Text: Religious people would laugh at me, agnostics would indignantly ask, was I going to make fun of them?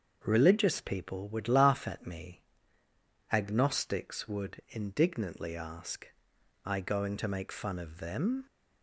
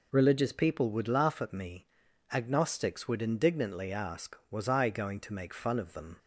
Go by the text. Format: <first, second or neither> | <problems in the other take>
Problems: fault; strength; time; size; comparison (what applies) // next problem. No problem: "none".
second | starts louder than the rest; until 1.2 s; 6.5 dB // skips "was"; at 6.3 s